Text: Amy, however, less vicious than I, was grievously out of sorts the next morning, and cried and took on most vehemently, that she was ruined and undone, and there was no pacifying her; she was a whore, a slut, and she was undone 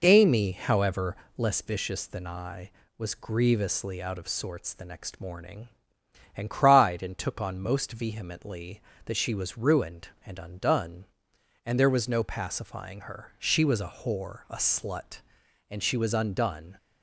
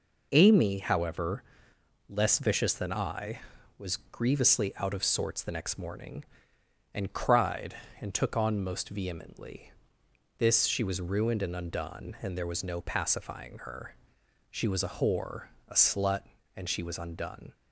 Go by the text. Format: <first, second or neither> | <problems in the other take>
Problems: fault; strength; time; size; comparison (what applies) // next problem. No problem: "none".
first | says "this" for "that"; at 10.3 s